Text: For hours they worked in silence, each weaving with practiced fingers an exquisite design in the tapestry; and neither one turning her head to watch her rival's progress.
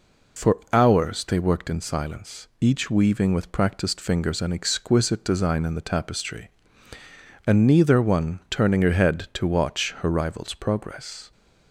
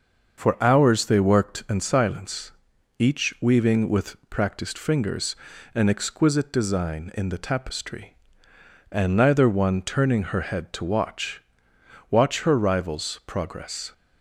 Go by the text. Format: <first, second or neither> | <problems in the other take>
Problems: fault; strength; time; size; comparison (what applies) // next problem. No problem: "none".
first | starts louder than the rest; until 1.5 s; 6 dB // pauses between "fingers" and "an"; at 5.3 s; 0.40 s long // says "watch" twice; at 12.0 s